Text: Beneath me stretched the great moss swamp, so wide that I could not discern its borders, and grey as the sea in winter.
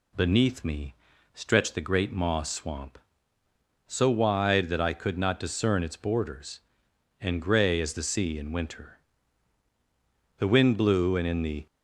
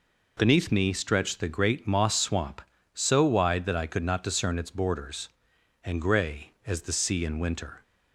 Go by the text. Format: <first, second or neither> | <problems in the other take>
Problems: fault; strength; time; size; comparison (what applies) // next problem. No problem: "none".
second | pauses between "me" and "stretched"; at 0.9 s; 0.40 s long // goes on to say "The wind blew and in the"; noticeable; from 10.3 s on; 1.2 s long